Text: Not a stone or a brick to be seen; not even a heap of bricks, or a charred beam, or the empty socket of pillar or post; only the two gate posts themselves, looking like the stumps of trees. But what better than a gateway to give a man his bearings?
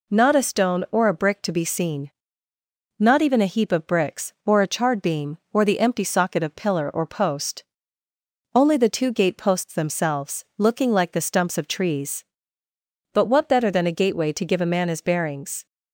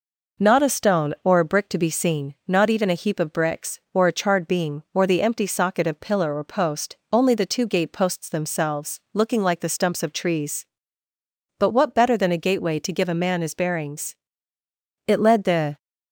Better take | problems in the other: first | goes on to say "It led the"; noticeable; from 15.0 s on; 0.70 s long

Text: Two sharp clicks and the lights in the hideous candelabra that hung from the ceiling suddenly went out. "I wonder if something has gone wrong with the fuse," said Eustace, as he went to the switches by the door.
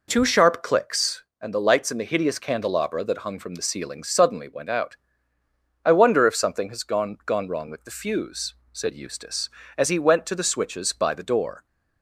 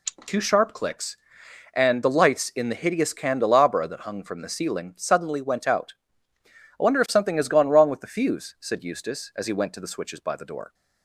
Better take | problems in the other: second | says "gone" twice; at 7.2 s

